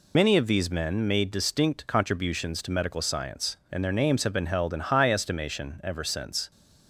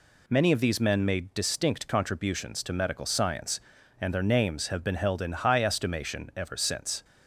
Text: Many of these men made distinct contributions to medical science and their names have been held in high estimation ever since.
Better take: second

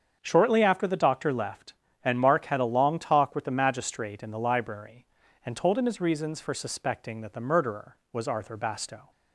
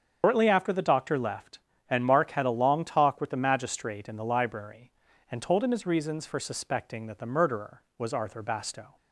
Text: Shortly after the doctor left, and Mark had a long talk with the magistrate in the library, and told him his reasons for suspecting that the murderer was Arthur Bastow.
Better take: first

